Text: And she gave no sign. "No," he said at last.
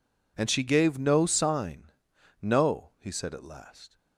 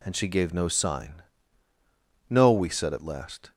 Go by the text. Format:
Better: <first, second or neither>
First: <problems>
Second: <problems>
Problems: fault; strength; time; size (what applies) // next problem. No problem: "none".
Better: first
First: none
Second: says "we" for "he"; at 2.5 s